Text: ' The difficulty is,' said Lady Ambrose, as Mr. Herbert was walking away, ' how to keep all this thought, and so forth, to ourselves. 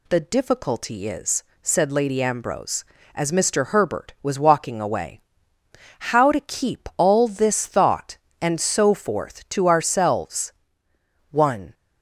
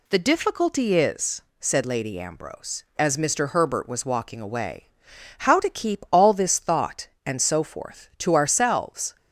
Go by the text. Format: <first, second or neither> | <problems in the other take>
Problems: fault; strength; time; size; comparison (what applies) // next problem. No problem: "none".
second | goes on to say "One"; slight; from 11.3 s on; 0.42 s long